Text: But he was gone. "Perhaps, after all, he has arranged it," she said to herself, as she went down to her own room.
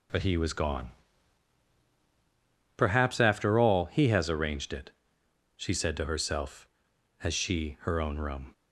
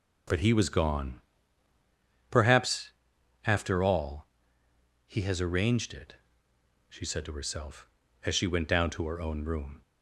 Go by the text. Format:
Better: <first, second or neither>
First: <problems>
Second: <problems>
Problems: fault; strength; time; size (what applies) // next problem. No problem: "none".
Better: second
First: skips "went down to"; at 7.7 s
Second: none